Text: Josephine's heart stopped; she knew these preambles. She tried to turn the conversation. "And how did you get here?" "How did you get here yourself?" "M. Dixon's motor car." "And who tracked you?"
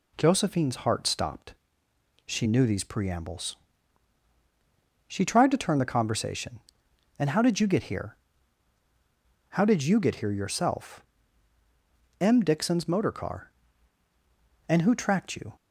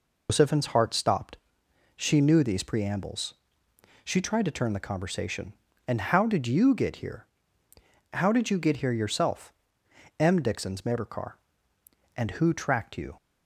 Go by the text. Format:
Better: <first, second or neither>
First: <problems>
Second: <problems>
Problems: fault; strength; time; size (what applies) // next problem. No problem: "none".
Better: first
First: none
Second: loses the start of "Josephine's"; at 0.2 s; 145 ms